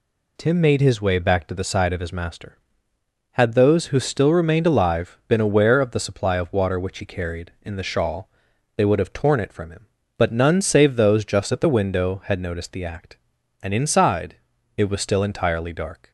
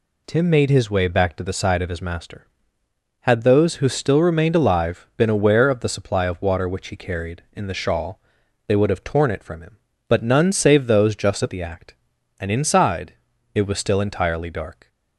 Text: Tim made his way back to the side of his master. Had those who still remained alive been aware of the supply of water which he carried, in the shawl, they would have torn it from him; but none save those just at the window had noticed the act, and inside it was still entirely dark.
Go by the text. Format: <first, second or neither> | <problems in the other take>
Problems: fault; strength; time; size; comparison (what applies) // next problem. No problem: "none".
first | skips "the window had noticed"; at 11.5 s // pauses between "inside" and "it"; at 13.1 s; 0.40 s long; also in the first